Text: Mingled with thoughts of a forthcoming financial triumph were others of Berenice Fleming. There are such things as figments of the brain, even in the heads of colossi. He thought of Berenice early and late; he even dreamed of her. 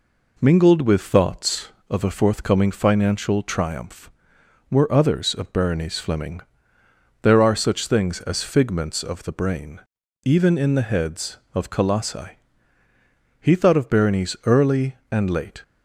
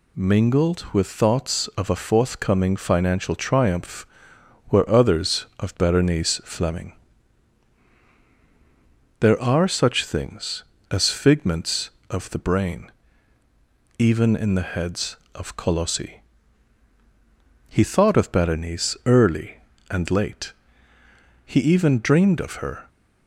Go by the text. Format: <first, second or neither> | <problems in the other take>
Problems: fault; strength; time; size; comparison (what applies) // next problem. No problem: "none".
second | stops before "he even dreamed of her"; at 15.6 s